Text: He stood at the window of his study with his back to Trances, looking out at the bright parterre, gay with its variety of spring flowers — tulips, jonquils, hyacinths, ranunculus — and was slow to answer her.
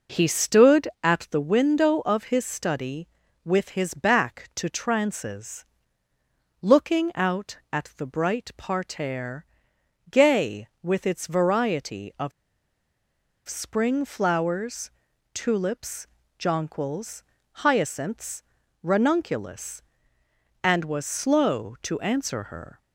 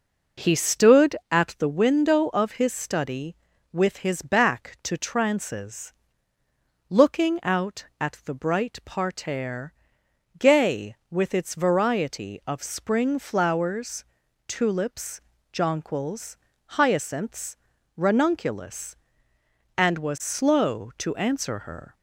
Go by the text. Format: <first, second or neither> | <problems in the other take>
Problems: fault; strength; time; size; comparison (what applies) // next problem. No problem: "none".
second | pauses between "of" and "spring"; at 12.3 s; 1.1 s long